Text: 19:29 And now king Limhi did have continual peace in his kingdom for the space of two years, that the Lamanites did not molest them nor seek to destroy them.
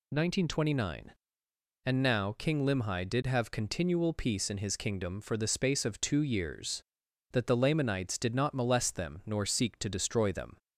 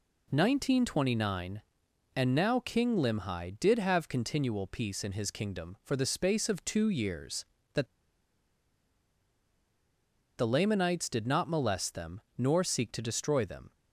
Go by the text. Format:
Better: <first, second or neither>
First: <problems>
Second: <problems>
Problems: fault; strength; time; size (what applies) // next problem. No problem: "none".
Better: first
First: none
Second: pauses between "that" and "the"; strong; at 7.8 s; 2.5 s long // pauses between "them" and "nor"; slight; at 12.2 s; 0.16 s long